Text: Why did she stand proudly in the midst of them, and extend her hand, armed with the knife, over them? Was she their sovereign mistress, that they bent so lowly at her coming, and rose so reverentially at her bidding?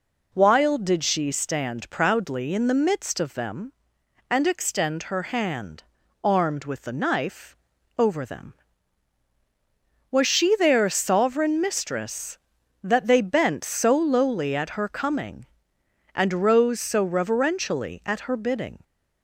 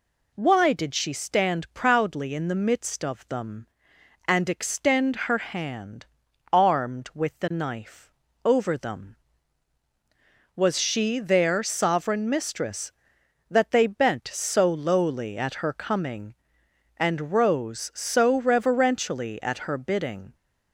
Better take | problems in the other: second | says "While" for "Why"; at 0.3 s

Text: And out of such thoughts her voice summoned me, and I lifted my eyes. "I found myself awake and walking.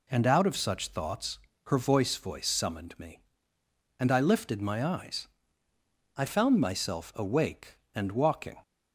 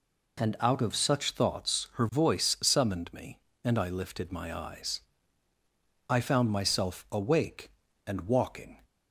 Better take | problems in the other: second | pauses between "thoughts" and "her"; slight; at 1.3 s; 0.26 s long // says "voice" twice; at 2.1 s

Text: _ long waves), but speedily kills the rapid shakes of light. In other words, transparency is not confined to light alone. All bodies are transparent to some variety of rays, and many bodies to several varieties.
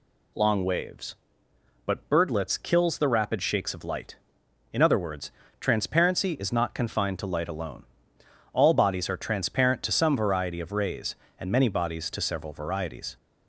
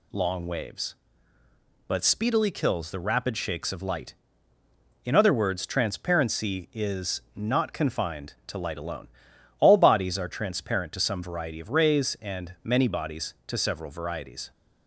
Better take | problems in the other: second | says "birdlets" for "speedily"; at 2.1 s

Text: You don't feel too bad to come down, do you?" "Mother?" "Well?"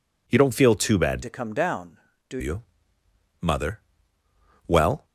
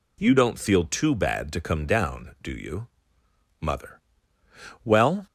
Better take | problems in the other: second | changes voice from "to" to "do"; from 1.2 to 2.3 s; 1.1 s long

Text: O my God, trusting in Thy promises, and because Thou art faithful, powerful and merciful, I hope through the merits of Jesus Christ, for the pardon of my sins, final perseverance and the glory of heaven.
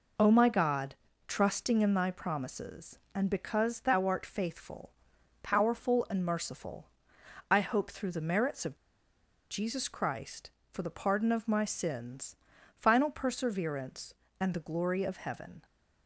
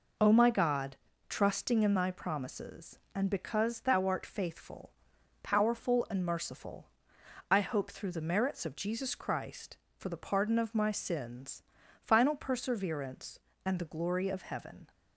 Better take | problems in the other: second | pauses between "of" and "Jesus"; noticeable; at 8.7 s; 0.74 s long

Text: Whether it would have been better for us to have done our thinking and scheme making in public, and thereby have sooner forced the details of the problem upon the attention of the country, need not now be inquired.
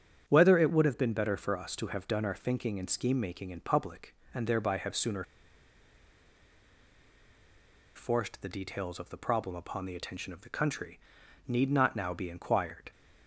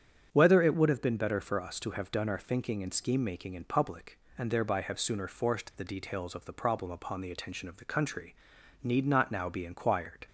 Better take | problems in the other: second | starts louder than the rest; strong; until 1.3 s; 8.5 dB; strong in the second // pauses between "sooner" and "forced"; strong; at 5.2 s; 2.7 s long

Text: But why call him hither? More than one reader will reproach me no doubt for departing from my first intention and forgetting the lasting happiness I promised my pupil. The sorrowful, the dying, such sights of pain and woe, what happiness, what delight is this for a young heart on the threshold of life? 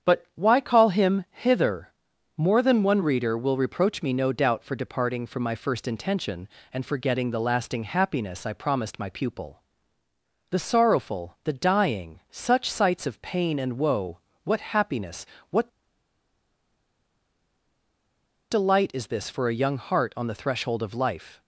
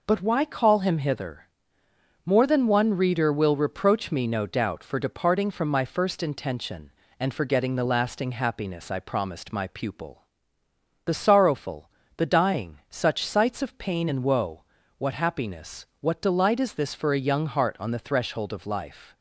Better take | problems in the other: second | starts louder than the rest; strong; until 1.1 s; 8 dB // pauses between "what" and "delight"; strong; at 15.6 s; 2.8 s long

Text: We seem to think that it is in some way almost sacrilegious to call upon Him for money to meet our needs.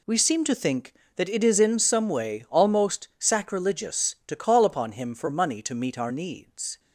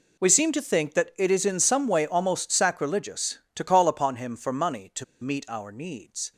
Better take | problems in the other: first | pauses between "to" and "meet"; slight; at 5.0 s; 0.17 s long

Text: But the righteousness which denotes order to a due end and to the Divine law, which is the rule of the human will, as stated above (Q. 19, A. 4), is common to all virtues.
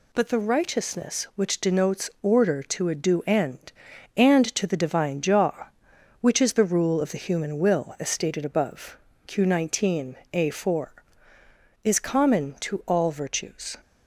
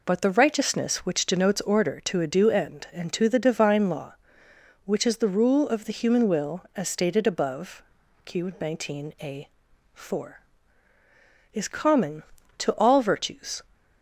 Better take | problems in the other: second | says "jaw" for "law"; at 5.2 s

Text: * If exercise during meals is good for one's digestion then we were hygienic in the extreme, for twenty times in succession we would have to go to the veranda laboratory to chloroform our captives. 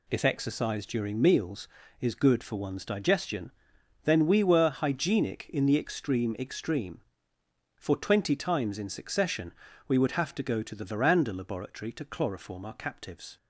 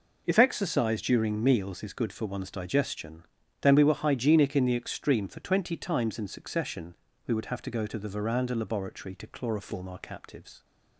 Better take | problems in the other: second | pauses between "digestion" and "then"; noticeable; at 3.5 s; 0.54 s long; slight in the second // says "extreme" twice; at 6.3 s // pauses between "succession" and "we"; at 9.5 s; 0.38 s long; slight in the second

